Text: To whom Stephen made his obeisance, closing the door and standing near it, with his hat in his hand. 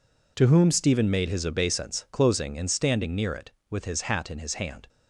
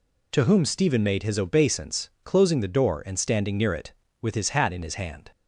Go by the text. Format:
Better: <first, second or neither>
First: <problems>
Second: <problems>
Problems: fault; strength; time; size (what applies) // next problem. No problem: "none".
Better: second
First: skips "the door"; at 2.5 s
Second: none